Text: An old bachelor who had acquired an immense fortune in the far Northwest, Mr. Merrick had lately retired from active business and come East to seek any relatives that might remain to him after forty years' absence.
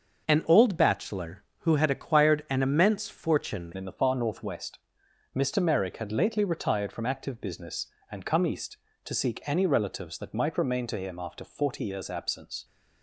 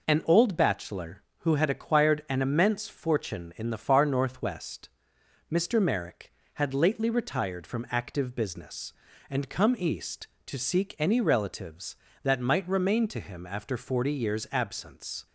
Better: second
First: starts louder than the rest; until 1.2 s; 6.5 dB // changes voice at "in"; from 3.7 s on; 8.9 s long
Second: none

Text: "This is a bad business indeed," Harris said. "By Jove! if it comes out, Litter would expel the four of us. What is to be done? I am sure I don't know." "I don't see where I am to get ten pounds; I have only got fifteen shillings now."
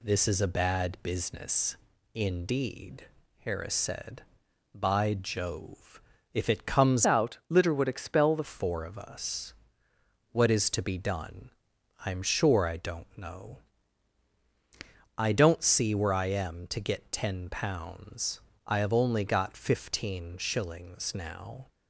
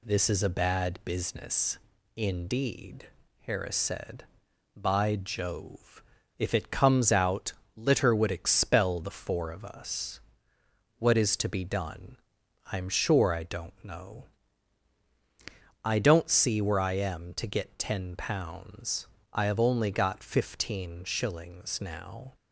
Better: second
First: pauses between "business" and "indeed"; slight; at 1.7 s; 0.36 s long // changes voice from "out" to "the"; from 7.0 to 8.4 s; 1.4 s long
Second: pauses between "business" and "indeed"; slight; at 1.7 s; 0.36 s long

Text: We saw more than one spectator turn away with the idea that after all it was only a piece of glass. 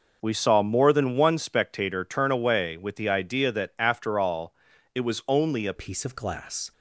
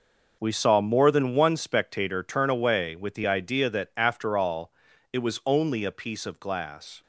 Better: second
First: pauses between "all" and "it"; at 4.5 s; 0.40 s long // changes voice at "piece"; from 5.7 s on; 1.0 s long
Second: pauses between "all" and "it"; at 4.7 s; 0.40 s long

